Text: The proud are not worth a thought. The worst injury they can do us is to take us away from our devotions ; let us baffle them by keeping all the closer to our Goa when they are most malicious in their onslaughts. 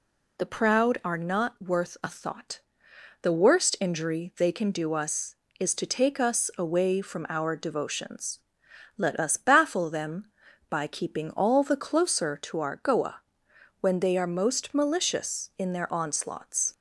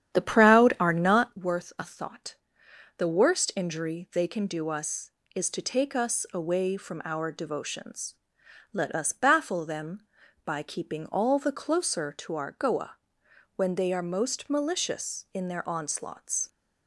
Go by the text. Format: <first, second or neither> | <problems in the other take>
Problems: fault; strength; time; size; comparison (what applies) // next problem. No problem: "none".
first | starts louder than the rest; strong; until 1.5 s; 10 dB // pauses between "Goa" and "when"; noticeable; at 12.9 s; 0.60 s long; noticeable in the first